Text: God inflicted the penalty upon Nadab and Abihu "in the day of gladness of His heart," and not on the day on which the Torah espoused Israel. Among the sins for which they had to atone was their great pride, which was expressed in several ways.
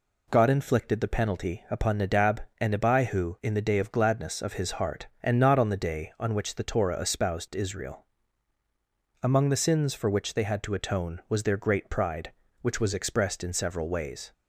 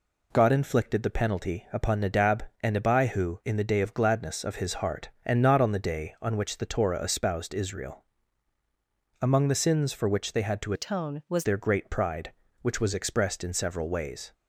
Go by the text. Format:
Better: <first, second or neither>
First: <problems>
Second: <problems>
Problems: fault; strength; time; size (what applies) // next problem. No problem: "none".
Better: first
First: none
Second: changes voice from "atone" to "was"; from 10.7 to 11.4 s; 0.7 s long